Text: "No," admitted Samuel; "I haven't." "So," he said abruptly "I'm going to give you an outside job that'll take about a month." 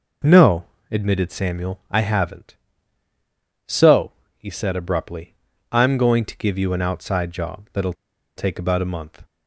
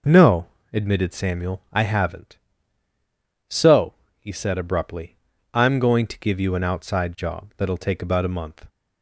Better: second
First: pauses between "abruptly" and "I'm"; slight; at 5.3 s; 0.34 s long // pauses between "that'll" and "take"; at 7.9 s; 0.43 s long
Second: pauses between "abruptly" and "I'm"; slight; at 5.1 s; 0.34 s long

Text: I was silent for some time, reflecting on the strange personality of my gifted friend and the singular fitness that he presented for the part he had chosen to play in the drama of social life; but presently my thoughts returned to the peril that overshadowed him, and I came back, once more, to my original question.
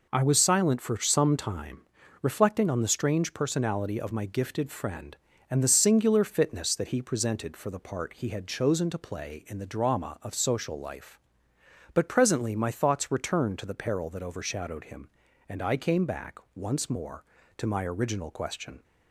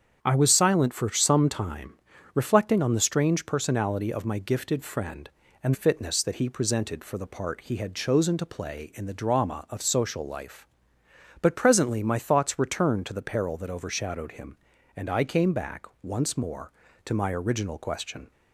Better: first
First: none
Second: starts louder than the rest; strong; until 1.2 s; 8 dB // skips "the singular"; at 5.7 s

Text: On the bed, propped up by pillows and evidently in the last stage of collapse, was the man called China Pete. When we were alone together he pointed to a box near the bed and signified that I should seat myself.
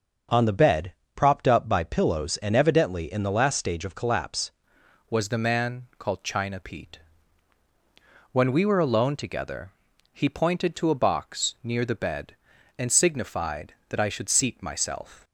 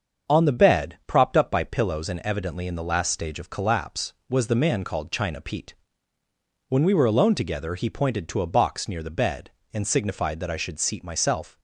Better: second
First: starts louder than the rest; until 1.5 s; 6.5 dB // changes voice at "was"; from 5.0 s on; 10.2 s long // pauses between "together" and "he"; at 9.7 s; 0.40 s long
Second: starts louder than the rest; until 1.3 s; 7 dB

